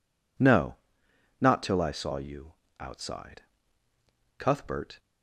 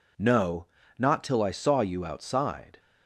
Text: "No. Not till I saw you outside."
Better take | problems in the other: second | pauses between "you" and "outside"; slight; at 2.5 s; 0.26 s long // goes on to say "Cuthbert"; noticeable; from 4.3 s on; 0.62 s long

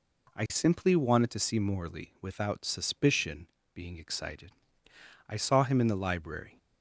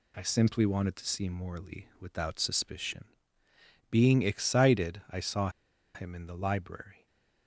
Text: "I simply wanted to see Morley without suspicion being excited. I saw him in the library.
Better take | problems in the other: first | pauses between "suspicion" and "being"; noticeable; at 3.0 s; 0.86 s long; slight in the first // pauses between "saw" and "him"; at 5.4 s; 0.45 s long // stays silent after the last word; slight; from 6.9 s on; 0.5 s long

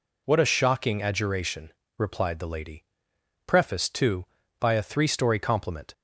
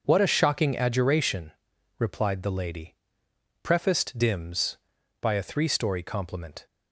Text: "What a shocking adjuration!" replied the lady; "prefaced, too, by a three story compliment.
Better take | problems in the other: first | says "dims" for "too"; at 4.1 s

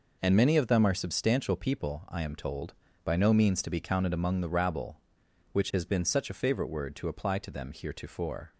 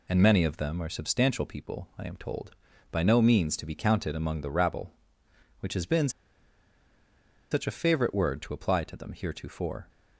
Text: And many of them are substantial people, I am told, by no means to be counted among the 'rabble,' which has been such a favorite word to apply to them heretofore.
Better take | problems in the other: first | pauses between "been" and "such"; strong; at 6.0 s; 1.4 s long

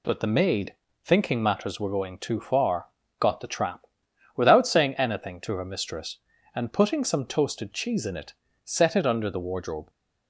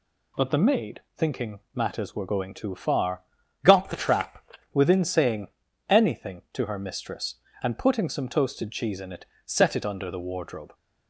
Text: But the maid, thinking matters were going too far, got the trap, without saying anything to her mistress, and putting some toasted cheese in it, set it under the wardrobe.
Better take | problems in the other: first | says "within" for "without"; at 4.7 s // pauses between "saying" and "anything"; at 5.4 s; 0.40 s long

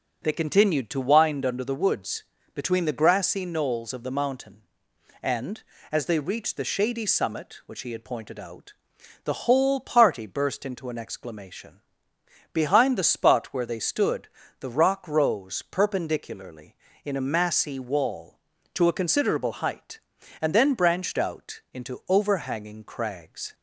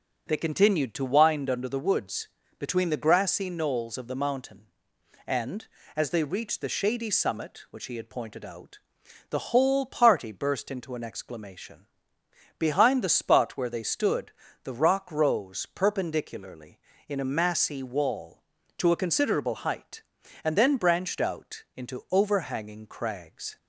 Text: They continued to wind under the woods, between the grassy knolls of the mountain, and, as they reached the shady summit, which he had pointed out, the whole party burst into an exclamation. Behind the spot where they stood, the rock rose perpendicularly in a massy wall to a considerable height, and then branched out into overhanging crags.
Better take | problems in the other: neither | none

